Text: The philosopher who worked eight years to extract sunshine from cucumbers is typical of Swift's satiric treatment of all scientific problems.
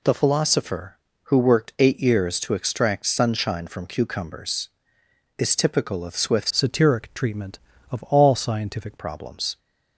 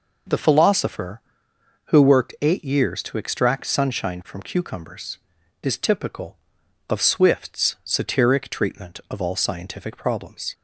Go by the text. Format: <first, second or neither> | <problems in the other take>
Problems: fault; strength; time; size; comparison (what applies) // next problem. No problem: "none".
second | changes voice from "satiric" to "scientific"; from 6.4 to 8.9 s; 2.5 s long